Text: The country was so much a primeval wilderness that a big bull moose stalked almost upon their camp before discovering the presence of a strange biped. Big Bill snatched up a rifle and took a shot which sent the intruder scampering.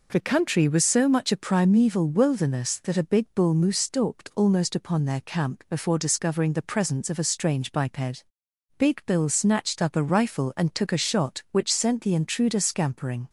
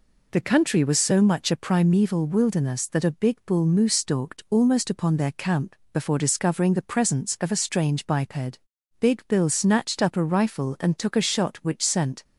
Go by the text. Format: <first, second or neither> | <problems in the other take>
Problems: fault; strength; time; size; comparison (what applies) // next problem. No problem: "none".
first | pauses between "camp" and "before"; slight; at 5.7 s; 0.20 s long // stops before "the intruder scampering"; at 12.2 s